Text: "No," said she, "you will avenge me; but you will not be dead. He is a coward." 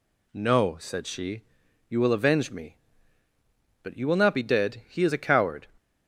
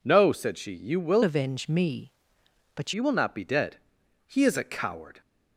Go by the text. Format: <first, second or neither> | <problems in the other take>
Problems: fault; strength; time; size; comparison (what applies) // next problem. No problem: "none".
first | changes voice from "avenge" to "but"; from 1.2 to 2.9 s; 1.7 s long